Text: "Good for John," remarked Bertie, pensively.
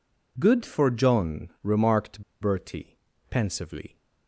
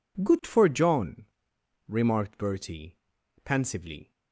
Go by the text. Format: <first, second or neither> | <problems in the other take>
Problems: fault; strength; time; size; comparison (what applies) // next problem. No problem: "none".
second | pauses between "remarked" and "Bertie"; slight; at 2.2 s; 0.18 s long